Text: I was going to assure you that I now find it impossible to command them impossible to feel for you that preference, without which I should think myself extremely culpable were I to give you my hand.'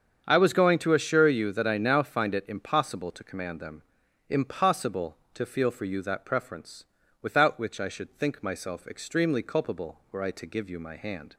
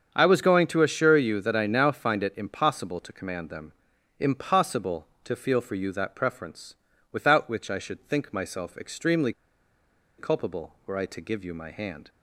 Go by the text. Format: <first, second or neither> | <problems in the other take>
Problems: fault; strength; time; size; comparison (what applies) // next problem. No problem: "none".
first | starts louder than the rest; strong; until 1.1 s; 7.5 dB; strong in the first // pauses between "them" and "impossible"; noticeable; at 3.7 s; 0.46 s long; noticeable in the first // pauses between "extremely" and "culpable"; noticeable; at 9.3 s; 0.86 s long